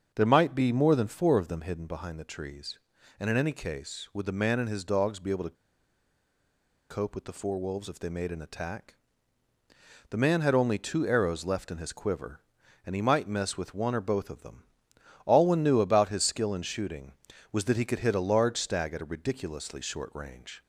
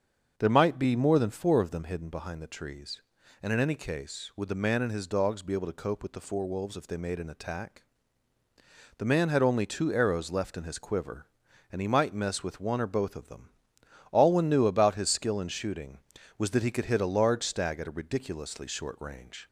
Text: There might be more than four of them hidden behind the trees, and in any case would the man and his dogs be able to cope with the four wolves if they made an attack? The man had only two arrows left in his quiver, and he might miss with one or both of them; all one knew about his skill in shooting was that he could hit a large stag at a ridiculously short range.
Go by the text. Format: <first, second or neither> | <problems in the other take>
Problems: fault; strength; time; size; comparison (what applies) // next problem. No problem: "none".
second | starts louder than the rest; until 1.1 s; 7 dB; also in the second // pauses between "to" and "cope"; strong; at 5.5 s; 1.3 s long